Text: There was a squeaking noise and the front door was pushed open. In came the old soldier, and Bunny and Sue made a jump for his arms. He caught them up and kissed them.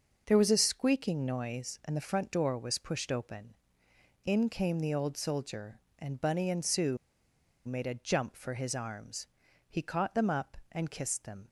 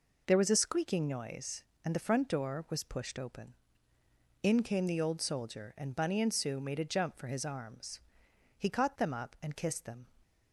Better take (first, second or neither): second